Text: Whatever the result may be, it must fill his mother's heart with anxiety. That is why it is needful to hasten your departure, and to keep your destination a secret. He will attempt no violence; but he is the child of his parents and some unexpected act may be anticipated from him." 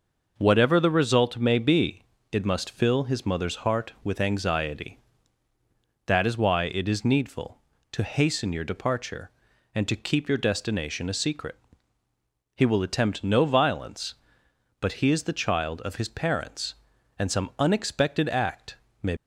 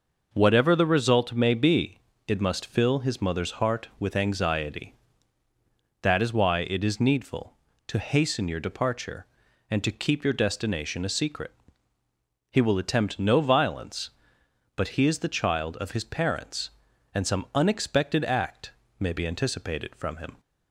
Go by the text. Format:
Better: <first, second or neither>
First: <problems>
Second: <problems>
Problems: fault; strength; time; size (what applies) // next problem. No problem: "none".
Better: second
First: pauses between "act" and "may"; slight; at 18.7 s; 0.26 s long // stops before "be anticipated from him"; at 19.1 s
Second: pauses between "act" and "may"; slight; at 18.7 s; 0.28 s long